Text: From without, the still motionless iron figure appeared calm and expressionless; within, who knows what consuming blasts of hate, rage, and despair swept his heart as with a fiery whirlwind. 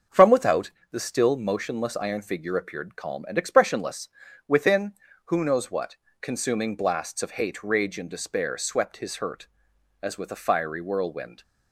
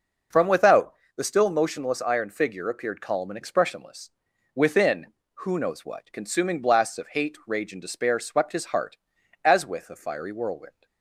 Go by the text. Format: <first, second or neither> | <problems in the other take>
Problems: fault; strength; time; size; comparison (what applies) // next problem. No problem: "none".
second | starts louder than the rest; until 1.3 s; 6.5 dB // pauses between "what" and "consuming"; slight; at 5.9 s; 0.26 s long // says "hurt" for "heart"; at 9.1 s